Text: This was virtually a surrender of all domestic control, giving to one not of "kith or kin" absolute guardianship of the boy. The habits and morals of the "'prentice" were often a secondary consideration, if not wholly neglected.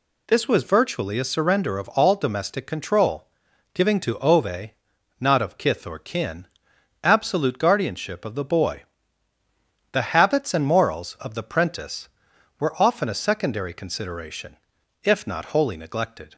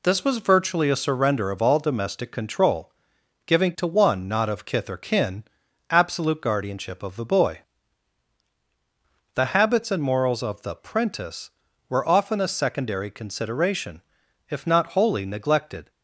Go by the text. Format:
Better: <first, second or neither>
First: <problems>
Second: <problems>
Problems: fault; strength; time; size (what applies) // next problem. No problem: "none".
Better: second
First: says "ove" for "one"; at 4.1 s // pauses between "kin" and "absolute"; noticeable; at 6.4 s; 0.56 s long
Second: pauses between "kin" and "absolute"; noticeable; at 5.4 s; 0.46 s long